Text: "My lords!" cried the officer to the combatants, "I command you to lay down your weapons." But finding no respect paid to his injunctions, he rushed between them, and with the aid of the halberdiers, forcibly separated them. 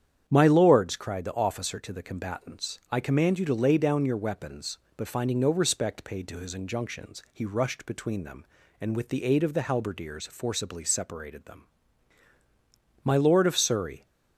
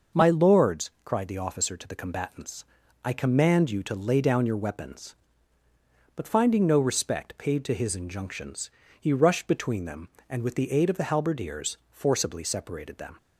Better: second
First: starts louder than the rest; strong; until 1.2 s; 9 dB // goes on to say "My lord of Surrey"; noticeable; from 13.0 s on; 1.0 s long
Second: none

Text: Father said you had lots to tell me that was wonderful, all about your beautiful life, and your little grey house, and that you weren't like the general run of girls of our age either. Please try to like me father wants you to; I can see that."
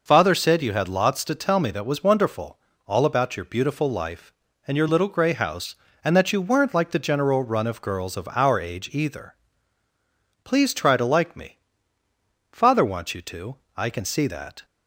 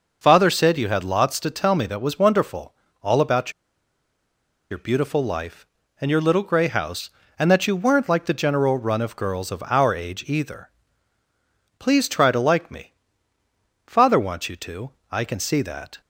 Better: first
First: pauses between "me" and "father"; noticeable; at 11.5 s; 0.94 s long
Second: pauses between "about" and "your"; at 3.5 s; 1.2 s long // pauses between "me" and "father"; noticeable; at 12.9 s; 0.94 s long

